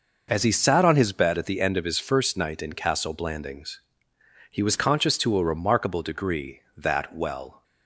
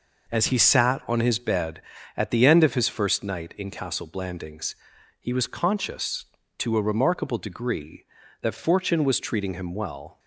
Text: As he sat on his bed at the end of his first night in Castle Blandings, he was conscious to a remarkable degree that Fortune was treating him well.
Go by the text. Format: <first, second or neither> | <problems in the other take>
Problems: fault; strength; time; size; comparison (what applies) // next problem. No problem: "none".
second | skips "Fortune was treating him"; at 7.1 s